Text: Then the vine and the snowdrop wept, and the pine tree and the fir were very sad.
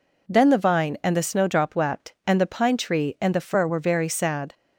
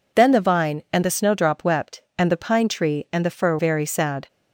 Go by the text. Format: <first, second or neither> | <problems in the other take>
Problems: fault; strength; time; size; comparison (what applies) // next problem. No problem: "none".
first | skips "were"; at 3.5 s